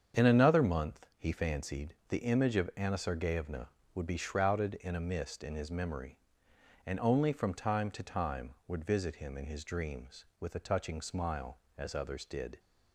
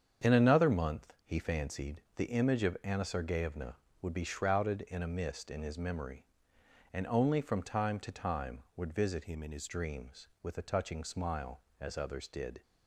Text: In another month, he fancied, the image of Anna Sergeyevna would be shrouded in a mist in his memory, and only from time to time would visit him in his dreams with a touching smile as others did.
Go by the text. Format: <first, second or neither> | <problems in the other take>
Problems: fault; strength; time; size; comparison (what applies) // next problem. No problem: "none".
first | starts louder than the rest; strong; until 1.3 s; 7.5 dB; strong in the first // changes voice from "him" to "his"; from 9.2 to 9.6 s; 0.4 s long